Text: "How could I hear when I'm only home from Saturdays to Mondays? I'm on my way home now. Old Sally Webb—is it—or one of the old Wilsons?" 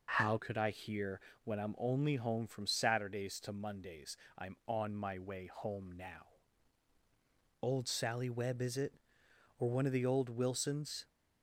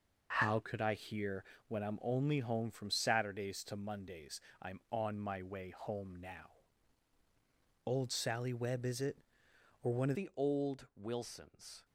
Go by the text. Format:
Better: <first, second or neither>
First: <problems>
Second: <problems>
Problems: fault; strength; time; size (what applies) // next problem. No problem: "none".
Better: first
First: pauses between "hear" and "when"; slight; at 1.1 s; 0.24 s long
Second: pauses between "hear" and "when"; slight; at 1.4 s; 0.24 s long // changes voice at "the"; from 10.1 s on; 1.7 s long